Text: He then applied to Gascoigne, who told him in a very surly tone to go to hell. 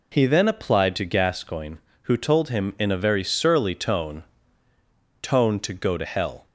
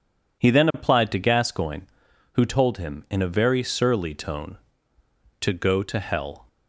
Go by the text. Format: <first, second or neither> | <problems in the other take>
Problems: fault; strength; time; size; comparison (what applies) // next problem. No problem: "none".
second | says "tone" twice; at 5.2 s